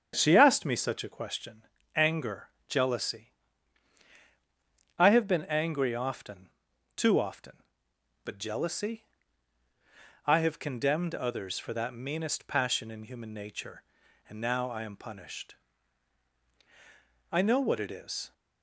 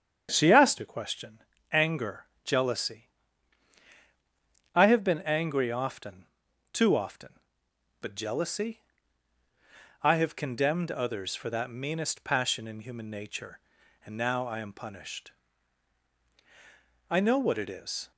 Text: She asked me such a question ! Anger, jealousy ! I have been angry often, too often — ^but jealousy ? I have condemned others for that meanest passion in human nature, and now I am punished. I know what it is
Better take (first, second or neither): first